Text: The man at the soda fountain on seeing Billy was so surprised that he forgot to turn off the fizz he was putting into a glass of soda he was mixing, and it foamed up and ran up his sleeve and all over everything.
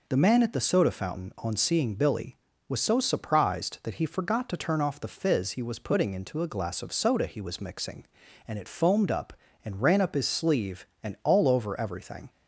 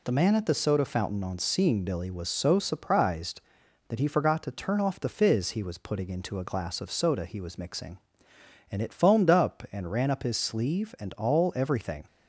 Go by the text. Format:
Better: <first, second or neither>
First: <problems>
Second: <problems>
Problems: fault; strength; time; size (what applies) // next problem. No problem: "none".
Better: first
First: none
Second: skips "over"; at 11.5 s